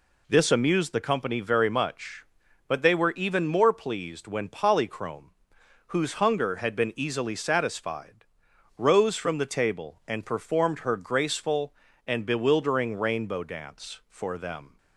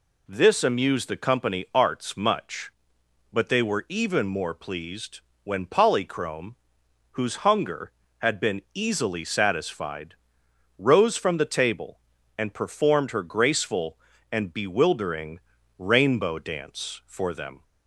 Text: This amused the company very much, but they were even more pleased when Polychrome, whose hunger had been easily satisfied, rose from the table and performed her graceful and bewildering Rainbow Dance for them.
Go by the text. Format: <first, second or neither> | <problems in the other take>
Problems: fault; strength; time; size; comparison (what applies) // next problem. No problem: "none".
first | says "arts" for "very"; at 1.7 s // pauses between "pleased" and "when"; slight; at 5.2 s; 0.24 s long // pauses between "bewildering" and "Rainbow"; slight; at 15.4 s; 0.36 s long